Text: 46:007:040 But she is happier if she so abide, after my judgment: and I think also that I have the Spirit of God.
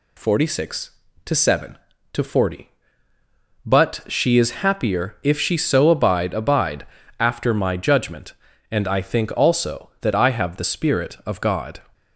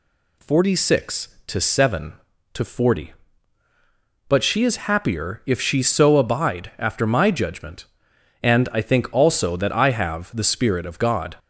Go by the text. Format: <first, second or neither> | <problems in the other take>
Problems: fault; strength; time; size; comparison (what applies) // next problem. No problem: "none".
second | says "abide" twice; at 6.3 s